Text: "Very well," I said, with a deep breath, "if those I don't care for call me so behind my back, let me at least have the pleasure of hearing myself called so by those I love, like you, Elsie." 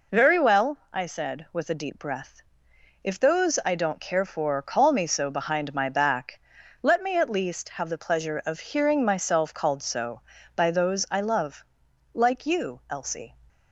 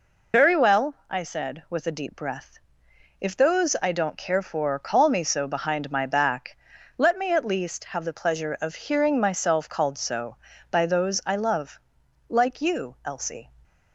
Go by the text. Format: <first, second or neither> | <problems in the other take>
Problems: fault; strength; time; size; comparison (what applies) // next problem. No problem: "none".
first | loses the start of "Very"; at 0.3 s; 55 ms